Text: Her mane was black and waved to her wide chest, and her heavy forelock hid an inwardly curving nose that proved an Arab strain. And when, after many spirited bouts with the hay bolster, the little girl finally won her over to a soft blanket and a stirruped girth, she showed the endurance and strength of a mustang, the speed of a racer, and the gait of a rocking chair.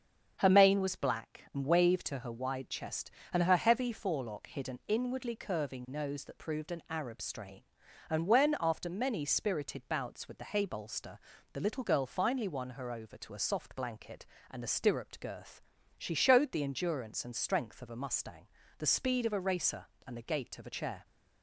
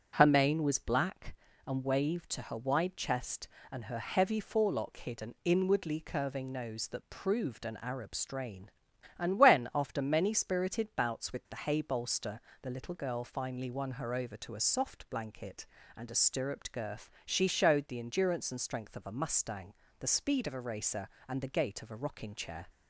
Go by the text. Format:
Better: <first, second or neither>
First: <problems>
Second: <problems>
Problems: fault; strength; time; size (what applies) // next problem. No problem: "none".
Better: second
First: starts louder than the rest; strong; until 1.4 s; 7.5 dB // skips "rocking"; at 20.7 s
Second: starts louder than the rest; strong; until 1.1 s; 8 dB